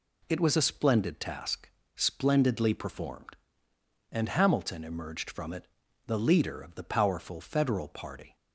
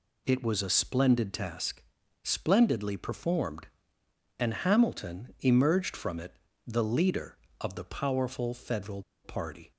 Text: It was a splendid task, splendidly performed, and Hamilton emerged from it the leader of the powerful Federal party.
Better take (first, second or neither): first